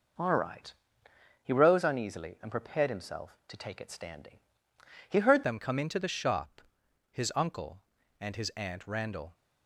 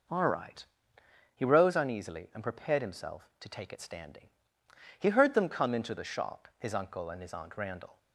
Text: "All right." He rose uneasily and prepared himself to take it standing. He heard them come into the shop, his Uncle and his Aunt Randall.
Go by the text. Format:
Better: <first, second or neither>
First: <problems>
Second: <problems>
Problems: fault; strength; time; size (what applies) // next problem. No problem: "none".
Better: second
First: changes voice at "them"; from 5.4 s on; 3.9 s long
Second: none